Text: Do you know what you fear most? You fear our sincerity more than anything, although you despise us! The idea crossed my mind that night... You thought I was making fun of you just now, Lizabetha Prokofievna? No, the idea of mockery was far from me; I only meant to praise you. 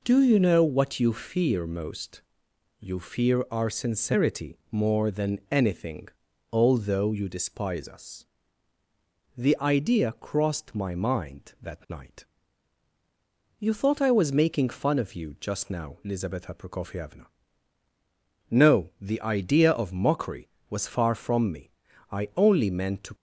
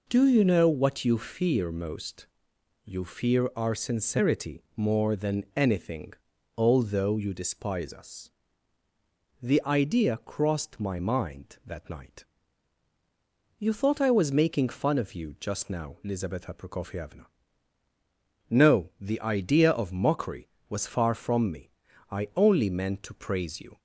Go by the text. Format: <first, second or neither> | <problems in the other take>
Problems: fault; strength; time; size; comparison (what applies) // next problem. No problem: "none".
second | stops before "praise you"; at 23.1 s